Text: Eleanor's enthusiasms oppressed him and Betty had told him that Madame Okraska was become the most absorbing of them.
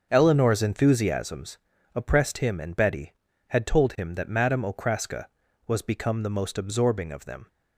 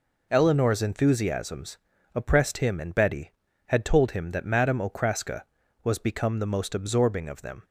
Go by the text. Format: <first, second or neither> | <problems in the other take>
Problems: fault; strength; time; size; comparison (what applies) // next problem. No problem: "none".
second | starts louder than the rest; until 1.5 s; 6.5 dB // pauses between "enthusiasms" and "oppressed"; at 1.5 s; 0.38 s long; also in the second